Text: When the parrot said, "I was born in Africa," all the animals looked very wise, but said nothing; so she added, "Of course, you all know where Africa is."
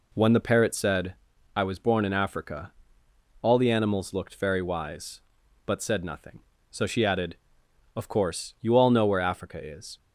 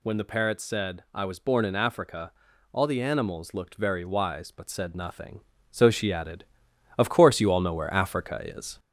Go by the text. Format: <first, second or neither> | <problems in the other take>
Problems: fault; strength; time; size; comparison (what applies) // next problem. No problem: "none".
first | gets louder; slight; throughout; 3 dB